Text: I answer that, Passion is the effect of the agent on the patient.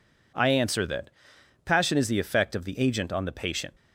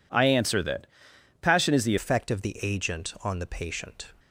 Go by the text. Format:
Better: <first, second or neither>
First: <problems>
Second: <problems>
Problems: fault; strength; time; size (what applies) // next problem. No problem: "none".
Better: first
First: none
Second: changes voice at "effect"; from 1.9 s on; 2.1 s long